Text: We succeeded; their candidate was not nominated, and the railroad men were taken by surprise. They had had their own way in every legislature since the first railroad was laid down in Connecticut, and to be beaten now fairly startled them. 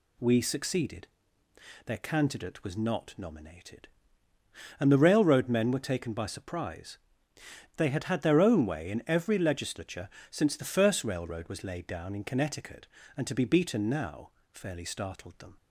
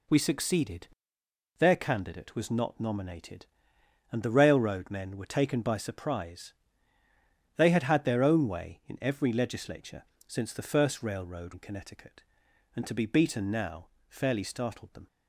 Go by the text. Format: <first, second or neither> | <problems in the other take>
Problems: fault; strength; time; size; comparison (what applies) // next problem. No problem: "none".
first | pauses between "legislature" and "since"; slight; at 10.0 s; 0.24 s long; slight in the first // skips "was laid down"; at 11.5 s // pauses between "now" and "fairly"; slight; at 13.8 s; 0.20 s long; slight in the first